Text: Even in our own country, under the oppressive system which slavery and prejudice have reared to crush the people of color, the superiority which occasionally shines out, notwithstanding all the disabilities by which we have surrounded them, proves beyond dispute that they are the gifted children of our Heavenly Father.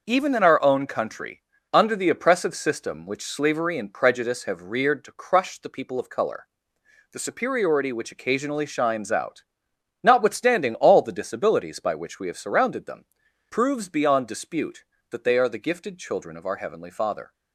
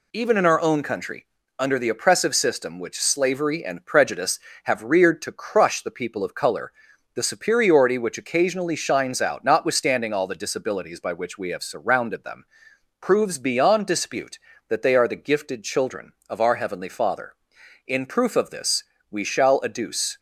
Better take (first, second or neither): first